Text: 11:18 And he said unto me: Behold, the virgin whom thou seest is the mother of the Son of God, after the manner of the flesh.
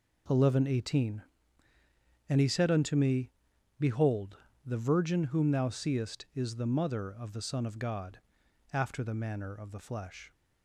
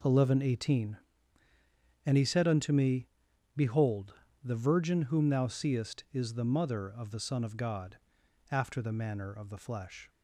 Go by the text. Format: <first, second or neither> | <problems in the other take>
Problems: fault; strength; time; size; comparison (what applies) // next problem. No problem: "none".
neither | none